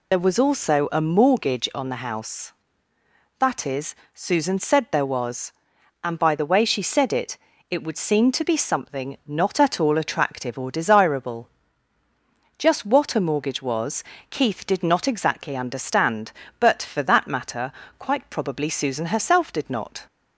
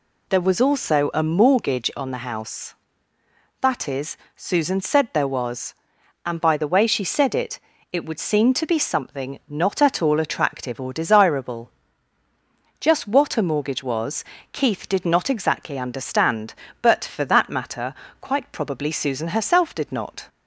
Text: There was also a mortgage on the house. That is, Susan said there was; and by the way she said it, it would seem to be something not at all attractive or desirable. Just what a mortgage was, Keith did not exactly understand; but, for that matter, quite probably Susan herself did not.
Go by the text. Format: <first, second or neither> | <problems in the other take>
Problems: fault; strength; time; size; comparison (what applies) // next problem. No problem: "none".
second | loses the start of "There"; at 0.1 s; 40 ms